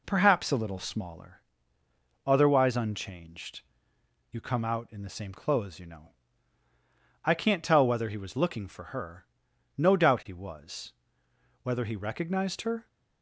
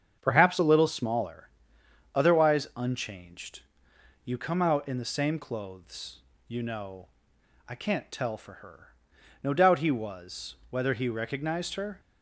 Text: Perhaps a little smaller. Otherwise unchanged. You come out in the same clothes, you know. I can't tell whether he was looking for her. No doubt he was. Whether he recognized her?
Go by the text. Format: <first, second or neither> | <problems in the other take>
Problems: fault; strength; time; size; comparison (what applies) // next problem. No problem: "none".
first | starts louder than the rest; strong; until 1.2 s; 7.5 dB // skips "whether he was looking"; at 8.3 s